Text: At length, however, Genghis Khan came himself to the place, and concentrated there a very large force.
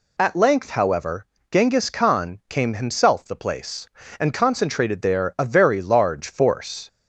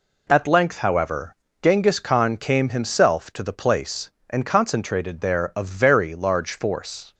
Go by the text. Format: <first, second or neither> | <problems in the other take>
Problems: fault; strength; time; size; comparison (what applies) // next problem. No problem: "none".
second | skips "to"; at 3.2 s